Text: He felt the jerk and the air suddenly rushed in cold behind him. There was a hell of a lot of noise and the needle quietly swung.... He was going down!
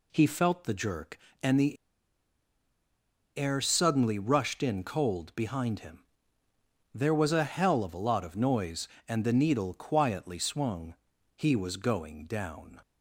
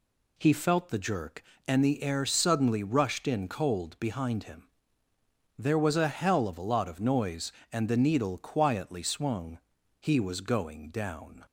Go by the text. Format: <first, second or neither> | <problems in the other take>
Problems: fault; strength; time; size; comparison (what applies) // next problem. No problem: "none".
second | pauses between "the" and "air"; strong; at 1.7 s; 1.6 s long